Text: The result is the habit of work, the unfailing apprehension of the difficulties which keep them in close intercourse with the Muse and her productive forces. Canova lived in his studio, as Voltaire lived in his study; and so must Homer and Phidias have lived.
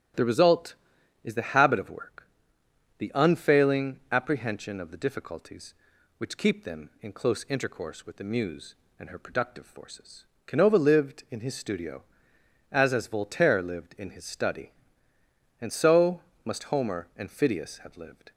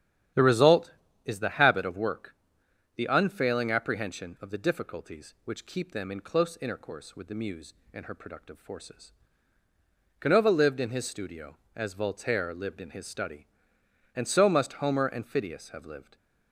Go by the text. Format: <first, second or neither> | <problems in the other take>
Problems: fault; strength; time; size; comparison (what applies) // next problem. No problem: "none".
second | starts louder than the rest; strong; until 1.6 s; 11.5 dB; strong in the second // says "as" twice; at 12.9 s // pauses between "so" and "must"; slight; at 16.1 s; 0.24 s long